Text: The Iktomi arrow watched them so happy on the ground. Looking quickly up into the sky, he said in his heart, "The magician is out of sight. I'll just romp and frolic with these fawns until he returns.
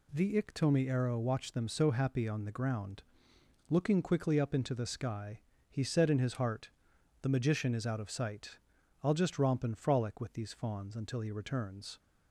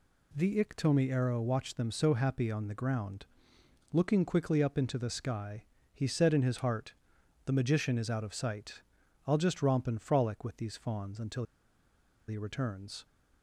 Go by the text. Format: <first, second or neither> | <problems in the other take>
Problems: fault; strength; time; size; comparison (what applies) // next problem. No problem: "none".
first | pauses between "until" and "he"; noticeable; at 11.4 s; 0.84 s long